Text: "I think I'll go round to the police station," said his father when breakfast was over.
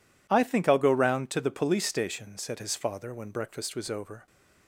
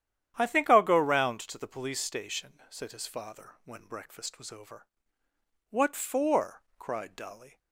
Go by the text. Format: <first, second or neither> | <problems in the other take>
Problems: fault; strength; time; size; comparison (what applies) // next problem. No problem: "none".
first | starts louder than the rest; strong; until 1.3 s; 10 dB // goes on to say "What for cried Dolly"; strong; from 5.6 s on; 1.9 s long